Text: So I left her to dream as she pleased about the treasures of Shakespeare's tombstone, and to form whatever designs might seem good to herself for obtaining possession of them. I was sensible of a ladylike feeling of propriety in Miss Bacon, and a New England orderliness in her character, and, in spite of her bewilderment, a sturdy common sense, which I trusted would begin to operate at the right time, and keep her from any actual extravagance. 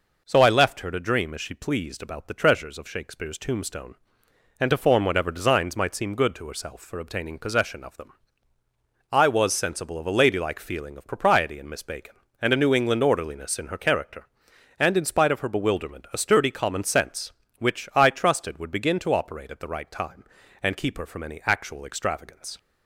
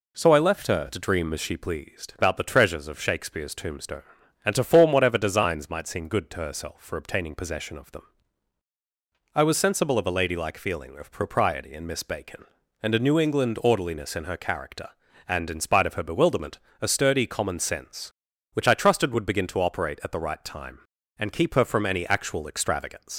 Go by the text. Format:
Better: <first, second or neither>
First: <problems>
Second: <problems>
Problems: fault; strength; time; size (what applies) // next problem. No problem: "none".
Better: first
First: none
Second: leaves "extravagance" unfinished; at 23.1 s; 70 ms